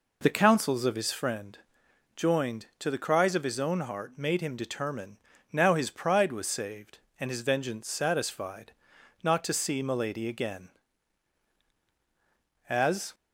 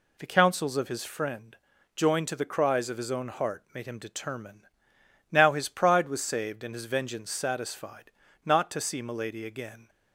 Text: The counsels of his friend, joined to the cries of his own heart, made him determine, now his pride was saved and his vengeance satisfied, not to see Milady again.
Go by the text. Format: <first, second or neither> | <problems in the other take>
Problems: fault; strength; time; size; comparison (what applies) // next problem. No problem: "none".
second | goes on to say "As"; slight; from 12.6 s on; 0.44 s long